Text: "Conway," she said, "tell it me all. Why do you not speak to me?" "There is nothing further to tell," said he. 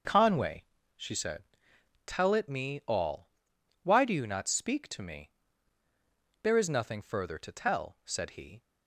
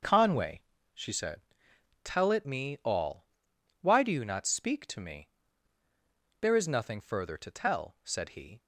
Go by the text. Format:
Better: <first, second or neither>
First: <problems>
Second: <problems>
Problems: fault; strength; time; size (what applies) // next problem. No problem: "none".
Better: neither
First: starts louder than the rest; until 1.3 s; 6 dB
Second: starts louder than the rest; until 1.3 s; 6 dB